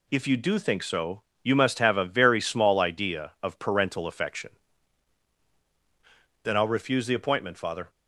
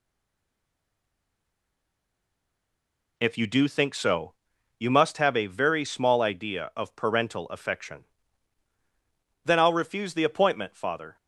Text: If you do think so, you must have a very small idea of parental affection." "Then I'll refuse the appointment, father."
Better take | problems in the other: first | stays silent before the first word; strong; until 3.1 s; 3.1 s long

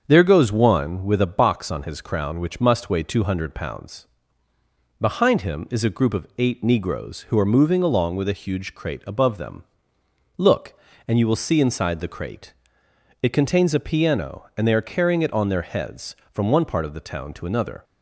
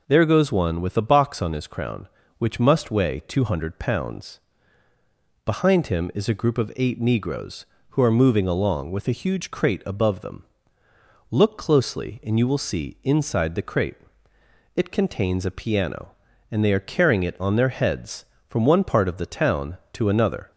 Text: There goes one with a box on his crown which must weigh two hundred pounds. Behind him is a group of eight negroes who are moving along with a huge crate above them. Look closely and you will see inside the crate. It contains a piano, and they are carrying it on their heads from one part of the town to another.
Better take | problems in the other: second | starts louder than the rest; until 1.0 s; 7 dB // skips "closely"; at 10.9 s

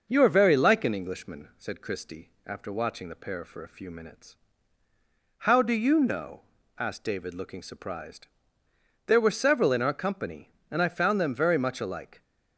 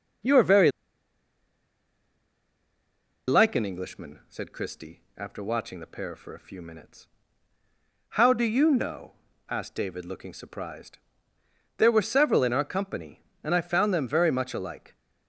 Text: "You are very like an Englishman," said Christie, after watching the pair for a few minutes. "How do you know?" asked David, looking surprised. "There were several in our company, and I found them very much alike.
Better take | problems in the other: first | starts louder than the rest; noticeable; until 3.8 s; 6 dB; noticeable in the first // pauses between "very" and "like"; strong; at 0.6 s; 2.5 s long

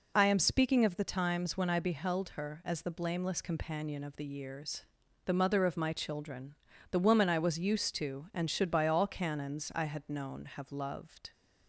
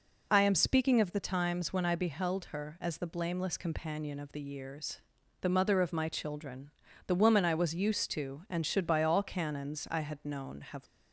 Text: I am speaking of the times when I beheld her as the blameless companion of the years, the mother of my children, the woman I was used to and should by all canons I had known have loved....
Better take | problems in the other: first | stops before "loved"; at 10.8 s

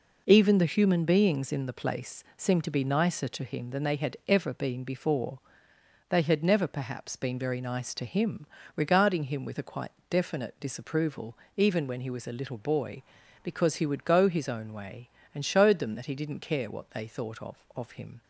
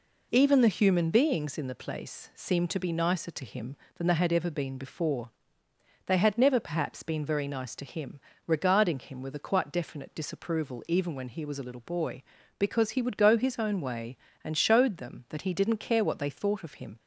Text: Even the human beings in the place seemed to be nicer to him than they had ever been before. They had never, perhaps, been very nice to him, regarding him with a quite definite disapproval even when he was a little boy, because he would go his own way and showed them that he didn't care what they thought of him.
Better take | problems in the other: second | pauses between "quite" and "definite"; slight; at 9.9 s; 0.20 s long // pauses between "disapproval" and "even"; slight; at 11.3 s; 0.20 s long // says "of" twice; at 17.7 s

